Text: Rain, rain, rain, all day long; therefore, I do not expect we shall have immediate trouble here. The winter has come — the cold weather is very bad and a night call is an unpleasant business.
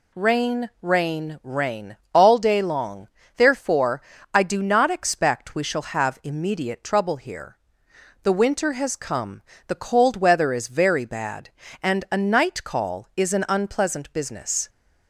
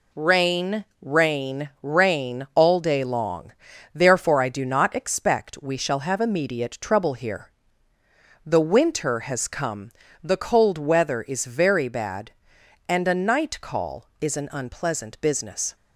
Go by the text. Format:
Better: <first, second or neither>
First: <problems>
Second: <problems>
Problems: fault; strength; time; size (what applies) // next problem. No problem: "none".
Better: neither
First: none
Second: none